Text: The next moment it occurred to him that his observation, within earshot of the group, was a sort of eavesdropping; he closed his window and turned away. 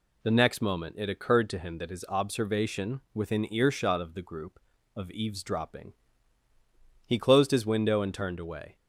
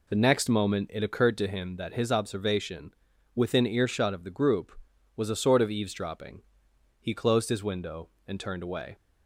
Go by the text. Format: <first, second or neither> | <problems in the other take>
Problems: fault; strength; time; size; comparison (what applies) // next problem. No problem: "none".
second | skips "was a sort"; at 4.7 s